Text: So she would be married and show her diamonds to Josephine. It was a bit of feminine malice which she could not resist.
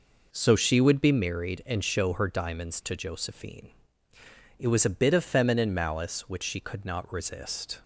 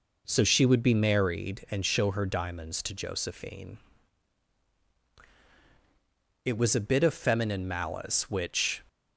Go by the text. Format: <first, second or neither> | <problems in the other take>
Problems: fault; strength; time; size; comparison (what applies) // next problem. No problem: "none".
first | stops before "she could not resist"; at 8.8 s